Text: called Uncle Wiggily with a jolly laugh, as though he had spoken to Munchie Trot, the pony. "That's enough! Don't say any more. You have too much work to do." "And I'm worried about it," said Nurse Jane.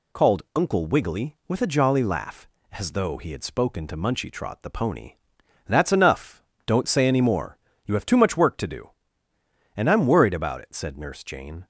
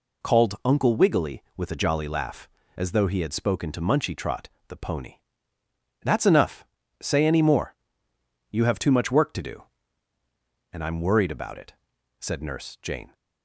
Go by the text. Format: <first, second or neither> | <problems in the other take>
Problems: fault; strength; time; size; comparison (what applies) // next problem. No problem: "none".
first | skips "Don't"; at 6.8 s